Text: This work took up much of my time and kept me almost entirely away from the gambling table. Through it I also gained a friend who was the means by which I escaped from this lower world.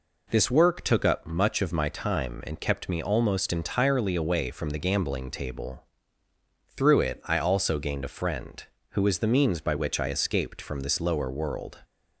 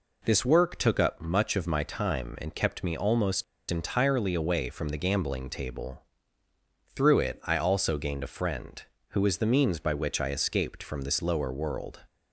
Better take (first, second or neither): first